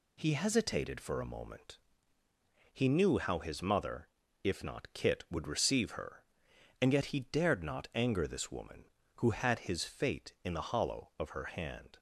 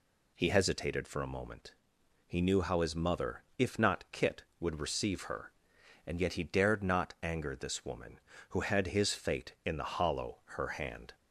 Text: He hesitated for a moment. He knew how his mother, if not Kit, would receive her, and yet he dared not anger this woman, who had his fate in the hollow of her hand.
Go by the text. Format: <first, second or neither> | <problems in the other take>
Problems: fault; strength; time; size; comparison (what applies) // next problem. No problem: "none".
first | skips "of"; at 10.4 s